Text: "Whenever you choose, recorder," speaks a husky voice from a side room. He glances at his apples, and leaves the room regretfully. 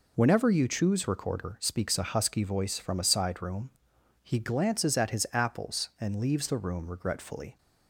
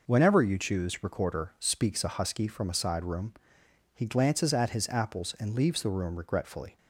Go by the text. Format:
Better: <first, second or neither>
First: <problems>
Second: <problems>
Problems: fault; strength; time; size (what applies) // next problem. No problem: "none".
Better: first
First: none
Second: skips "voice"; at 2.4 s